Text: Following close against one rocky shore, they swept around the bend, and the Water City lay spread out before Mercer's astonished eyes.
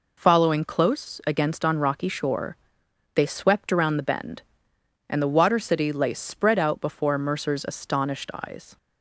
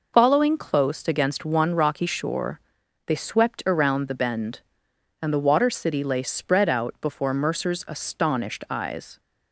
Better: second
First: says "on" for "one"; at 1.6 s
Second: none

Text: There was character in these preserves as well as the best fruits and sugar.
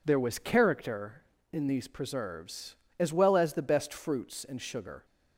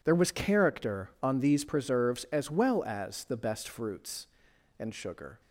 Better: first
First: none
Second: says "on" for "in"; at 1.2 s

